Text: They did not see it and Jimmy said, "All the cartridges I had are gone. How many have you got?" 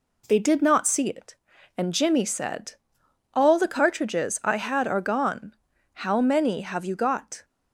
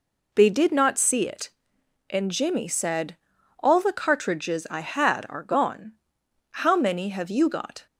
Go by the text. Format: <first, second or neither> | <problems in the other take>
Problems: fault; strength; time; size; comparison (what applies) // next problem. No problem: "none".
neither | none